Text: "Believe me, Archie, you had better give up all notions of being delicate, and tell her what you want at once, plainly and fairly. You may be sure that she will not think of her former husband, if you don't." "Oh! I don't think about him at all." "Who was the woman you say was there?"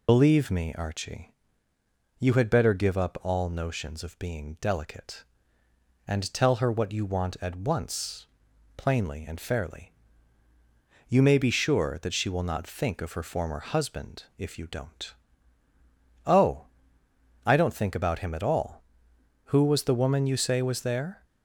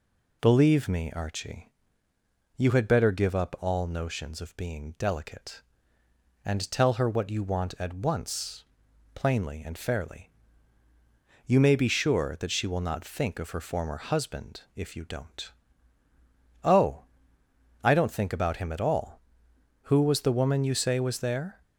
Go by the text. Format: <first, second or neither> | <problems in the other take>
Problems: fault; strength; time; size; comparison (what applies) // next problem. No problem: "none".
second | loses the start of "Believe"; at 0.0 s; 50 ms